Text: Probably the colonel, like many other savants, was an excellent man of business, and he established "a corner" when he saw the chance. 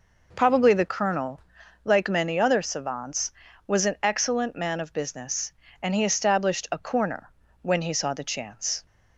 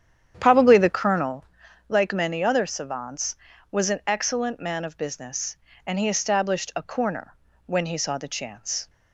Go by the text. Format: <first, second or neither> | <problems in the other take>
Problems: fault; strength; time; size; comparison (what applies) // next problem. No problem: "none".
first | starts louder than the rest; strong; until 1.4 s; 9 dB // pauses between "corner" and "when"; slight; at 7.3 s; 0.34 s long; slight in the first